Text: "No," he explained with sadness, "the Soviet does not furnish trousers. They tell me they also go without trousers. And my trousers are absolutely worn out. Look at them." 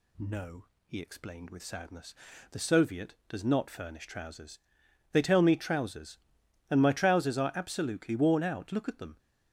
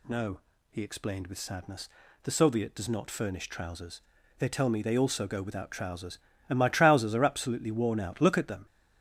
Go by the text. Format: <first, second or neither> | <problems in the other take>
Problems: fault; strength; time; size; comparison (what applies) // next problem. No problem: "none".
second | skips "they also go without"; at 5.5 s